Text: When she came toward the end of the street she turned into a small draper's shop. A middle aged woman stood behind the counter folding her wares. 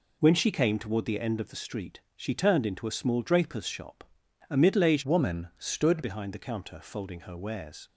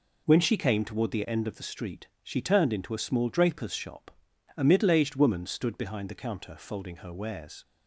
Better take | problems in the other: second | pauses between "street" and "she"; slight; at 2.0 s; 0.16 s long; slight in the second // changes voice from "woman" to "stood"; from 5.0 to 6.0 s; 1.0 s long

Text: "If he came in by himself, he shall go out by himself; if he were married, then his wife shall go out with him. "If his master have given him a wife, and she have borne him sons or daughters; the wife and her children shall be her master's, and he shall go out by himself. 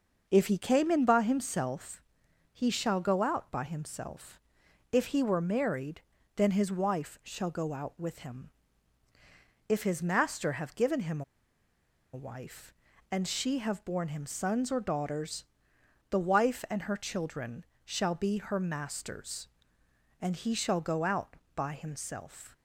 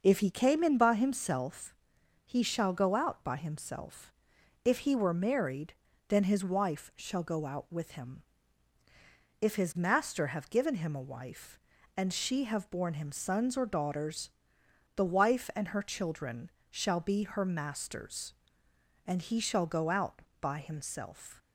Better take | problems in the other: second | pauses between "him" and "a"; noticeable; at 11.2 s; 0.91 s long // pauses between "children" and "shall"; slight; at 17.6 s; 0.18 s long; slight in the second

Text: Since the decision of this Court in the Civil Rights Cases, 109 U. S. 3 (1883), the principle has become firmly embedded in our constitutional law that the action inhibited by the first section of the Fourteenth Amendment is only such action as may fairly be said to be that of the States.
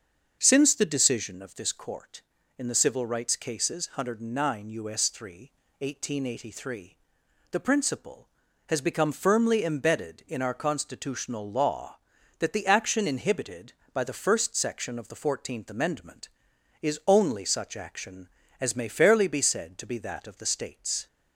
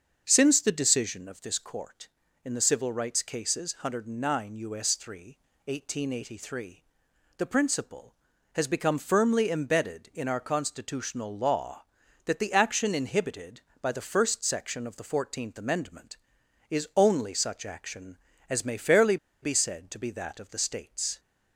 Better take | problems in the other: first | starts louder than the rest; until 1.2 s; 6.5 dB; also in the first // pauses between "fairly" and "be"; slight; at 19.1 s; 0.26 s long

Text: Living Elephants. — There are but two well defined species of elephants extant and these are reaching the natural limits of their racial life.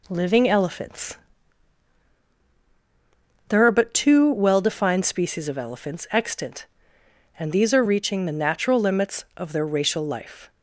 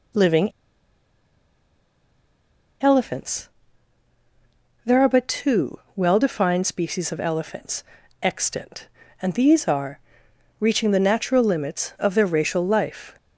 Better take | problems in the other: first | pauses between "Living" and "Elephants"; strong; at 0.5 s; 2.3 s long // pauses between "two" and "well"; slight; at 5.7 s; 0.18 s long // pauses between "elephants" and "extant"; slight; at 7.8 s; 0.36 s long // pauses between "are" and "reaching"; noticeable; at 9.9 s; 0.60 s long

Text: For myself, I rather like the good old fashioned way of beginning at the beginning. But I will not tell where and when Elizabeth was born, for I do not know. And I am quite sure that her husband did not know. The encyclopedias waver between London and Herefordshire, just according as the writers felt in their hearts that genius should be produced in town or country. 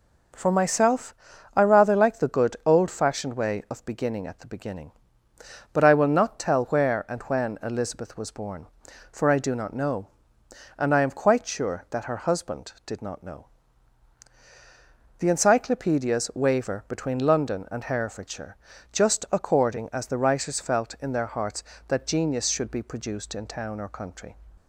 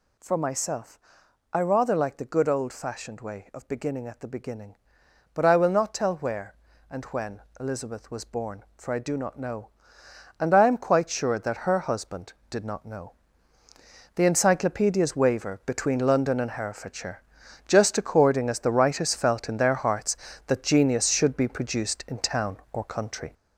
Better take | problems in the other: first | gets louder; throughout; 6.5 dB // pauses between "when" and "Elizabeth"; slight; at 7.4 s; 0.18 s long

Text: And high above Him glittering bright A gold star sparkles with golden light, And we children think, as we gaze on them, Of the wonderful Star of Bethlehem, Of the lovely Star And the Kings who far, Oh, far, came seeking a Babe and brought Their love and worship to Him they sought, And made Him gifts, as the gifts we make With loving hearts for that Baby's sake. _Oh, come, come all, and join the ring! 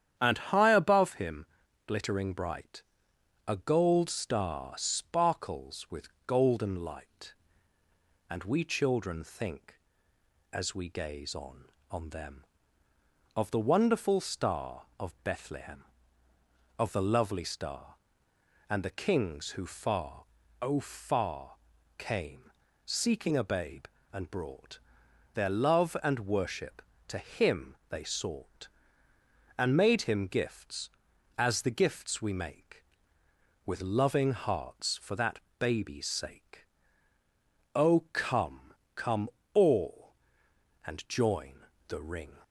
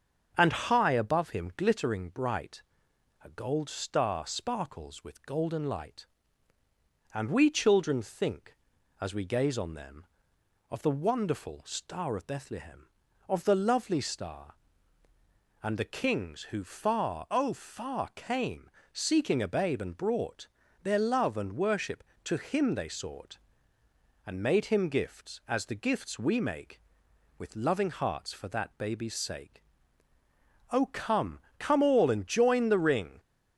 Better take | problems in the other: second | starts louder than the rest; strong; until 1.1 s; 9.5 dB; also in the second // pauses between "Him" and "glittering"; at 1.4 s; 0.40 s long // pauses between "bright" and "A"; noticeable; at 2.8 s; 0.66 s long; noticeable in the second // pauses between "with" and "golden"; slight; at 6.0 s; 0.16 s long // says "on" twice; at 11.9 s // pauses between "came" and "seeking"; slight; at 22.5 s; 0.36 s long; slight in the second // pauses between "brought" and "Their"; noticeable; at 24.7 s; 0.56 s long; slight in the second // pauses between "Him" and "they"; slight; at 27.7 s; 0.16 s long // pauses between "that" and "Baby's"; slight; at 35.3 s; 0.20 s long // pauses between "come" and "all"; slight; at 39.2 s; 0.24 s long // pauses between "join" and "the"; slight; at 41.5 s; 0.34 s long

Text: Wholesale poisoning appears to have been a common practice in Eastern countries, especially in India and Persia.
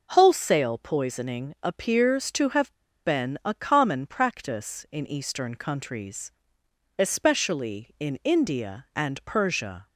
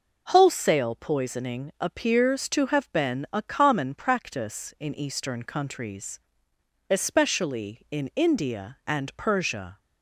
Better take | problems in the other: second | pauses between "have" and "been"; slight; at 2.7 s; 0.30 s long

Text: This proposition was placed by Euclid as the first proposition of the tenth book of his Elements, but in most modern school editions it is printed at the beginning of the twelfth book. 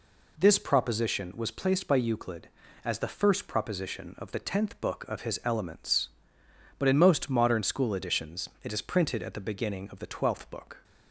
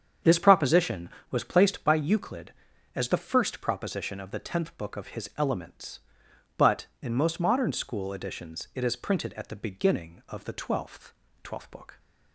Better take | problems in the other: first | starts louder than the rest; strong; until 1.4 s; 7.5 dB // says "twelfth" twice; at 11.4 s

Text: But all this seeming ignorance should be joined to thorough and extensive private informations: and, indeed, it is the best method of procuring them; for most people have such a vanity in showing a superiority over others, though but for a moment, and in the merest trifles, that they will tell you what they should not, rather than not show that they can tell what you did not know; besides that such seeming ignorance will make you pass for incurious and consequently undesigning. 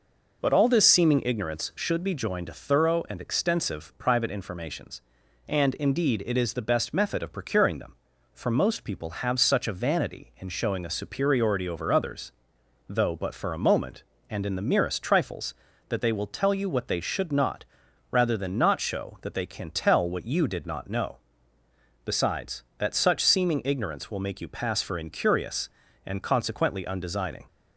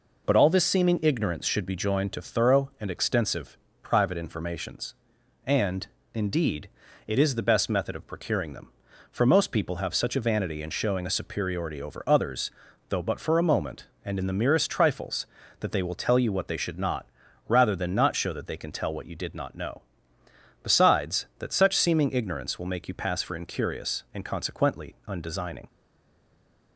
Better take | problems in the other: first | pauses between "extensive" and "private"; slight; at 3.5 s; 0.24 s long // stays silent after the last word; from 25.6 s on; 1.1 s long

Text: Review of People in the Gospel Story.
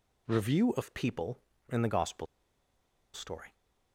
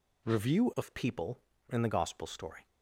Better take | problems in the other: second | pauses between "Gospel" and "Story"; noticeable; at 2.2 s; 0.88 s long

